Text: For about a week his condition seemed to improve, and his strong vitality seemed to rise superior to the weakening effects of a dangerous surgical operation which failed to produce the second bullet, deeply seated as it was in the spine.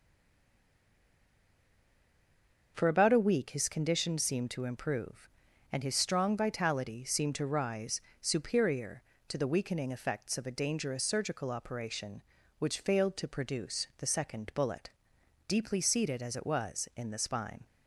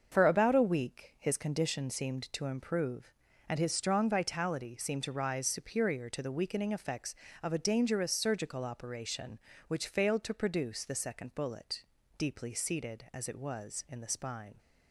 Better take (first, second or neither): second